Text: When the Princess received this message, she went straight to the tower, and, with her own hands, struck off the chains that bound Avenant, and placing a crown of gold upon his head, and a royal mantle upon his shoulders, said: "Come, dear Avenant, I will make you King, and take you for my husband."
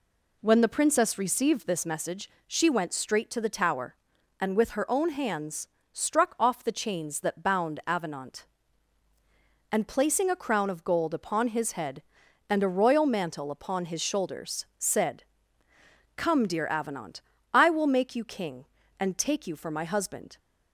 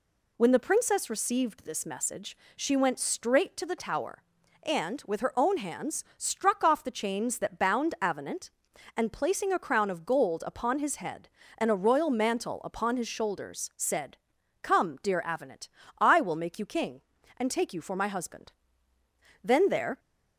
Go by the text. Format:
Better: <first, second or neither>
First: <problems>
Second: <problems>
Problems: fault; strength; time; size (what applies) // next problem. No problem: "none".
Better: first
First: none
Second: goes on to say "Then there"; from 19.4 s on; 0.56 s long